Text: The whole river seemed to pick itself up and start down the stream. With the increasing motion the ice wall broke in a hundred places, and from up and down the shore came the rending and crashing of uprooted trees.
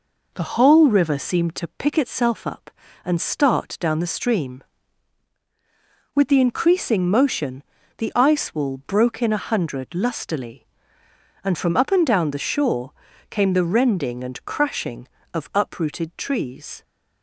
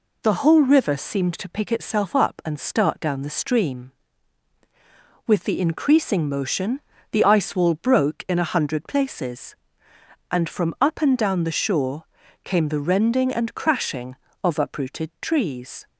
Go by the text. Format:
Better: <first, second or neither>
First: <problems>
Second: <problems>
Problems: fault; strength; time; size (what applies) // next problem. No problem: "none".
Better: second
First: pauses between "motion" and "the"; slight; at 7.6 s; 0.34 s long // says "lustily" for "places"; at 9.9 s // pauses between "shore" and "came"; at 12.9 s; 0.38 s long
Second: pauses between "motion" and "the"; slight; at 6.7 s; 0.32 s long // pauses between "shore" and "came"; at 12.0 s; 0.40 s long